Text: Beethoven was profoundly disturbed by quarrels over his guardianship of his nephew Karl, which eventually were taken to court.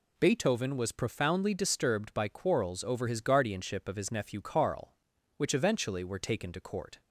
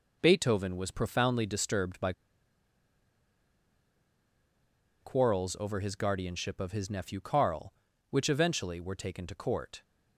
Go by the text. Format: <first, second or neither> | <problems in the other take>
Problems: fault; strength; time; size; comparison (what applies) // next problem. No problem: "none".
first | pauses between "by" and "quarrels"; strong; at 2.1 s; 2.9 s long